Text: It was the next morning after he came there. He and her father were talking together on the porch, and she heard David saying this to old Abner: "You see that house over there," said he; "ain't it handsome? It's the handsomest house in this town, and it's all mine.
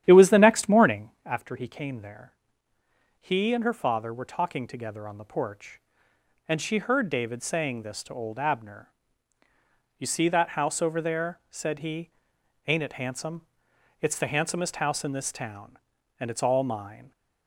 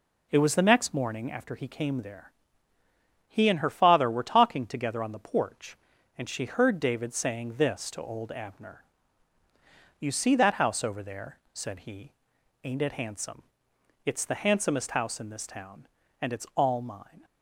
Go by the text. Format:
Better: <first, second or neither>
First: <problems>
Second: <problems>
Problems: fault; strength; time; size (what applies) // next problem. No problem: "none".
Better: second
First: starts louder than the rest; strong; until 1.2 s; 11 dB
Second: none